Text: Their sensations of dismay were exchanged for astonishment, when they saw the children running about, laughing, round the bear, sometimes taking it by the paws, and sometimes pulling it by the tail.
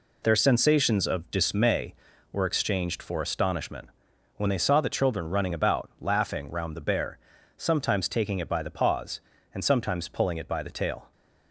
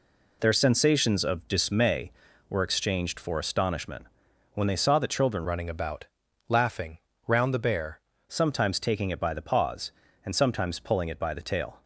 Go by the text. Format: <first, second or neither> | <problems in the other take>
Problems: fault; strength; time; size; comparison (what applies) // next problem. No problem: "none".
first | changes voice from "running" to "bear"; from 5.4 to 7.9 s; 2.5 s long